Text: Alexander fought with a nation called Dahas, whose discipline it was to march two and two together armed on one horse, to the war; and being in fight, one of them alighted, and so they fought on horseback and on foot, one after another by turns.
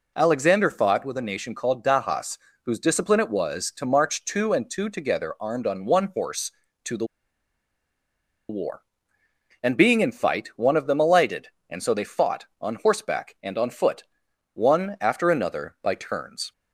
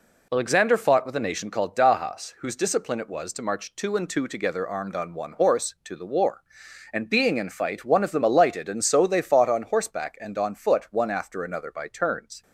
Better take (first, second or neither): second